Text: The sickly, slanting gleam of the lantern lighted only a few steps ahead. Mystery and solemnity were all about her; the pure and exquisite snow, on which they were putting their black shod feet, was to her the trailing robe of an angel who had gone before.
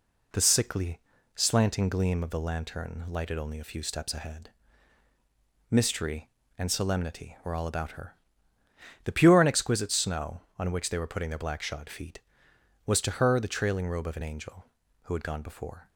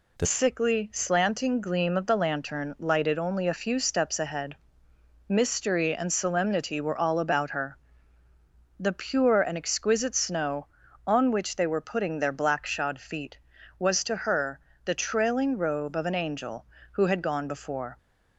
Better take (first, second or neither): first